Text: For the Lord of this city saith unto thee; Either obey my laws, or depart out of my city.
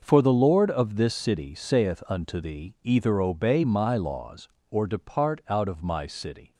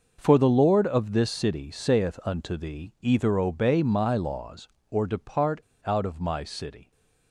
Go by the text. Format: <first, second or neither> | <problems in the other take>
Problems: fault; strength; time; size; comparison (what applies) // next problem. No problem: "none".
first | pauses between "depart" and "out"; slight; at 5.6 s; 0.21 s long